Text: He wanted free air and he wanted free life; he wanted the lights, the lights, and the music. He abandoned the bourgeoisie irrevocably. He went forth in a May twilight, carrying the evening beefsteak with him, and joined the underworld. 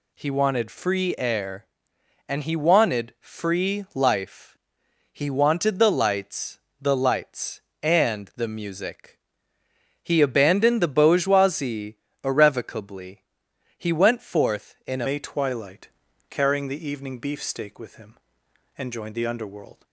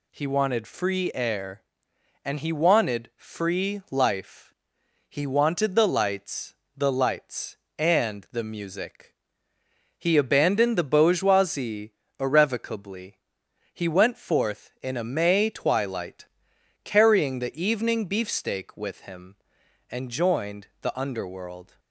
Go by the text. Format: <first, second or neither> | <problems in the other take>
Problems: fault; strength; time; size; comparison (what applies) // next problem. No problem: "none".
second | pauses between "bourgeoisie" and "irrevocably"; slight; at 11.9 s; 0.26 s long; slight in the second // changes voice at "May"; from 15.0 s on; 4.8 s long